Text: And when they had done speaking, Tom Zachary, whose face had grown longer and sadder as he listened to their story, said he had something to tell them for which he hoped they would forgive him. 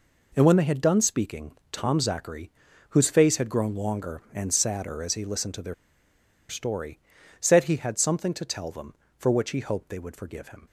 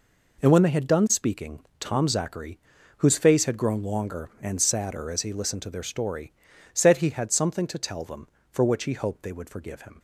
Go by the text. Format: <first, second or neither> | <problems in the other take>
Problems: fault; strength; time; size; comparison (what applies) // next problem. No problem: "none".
second | pauses between "their" and "story"; noticeable; at 5.7 s; 0.75 s long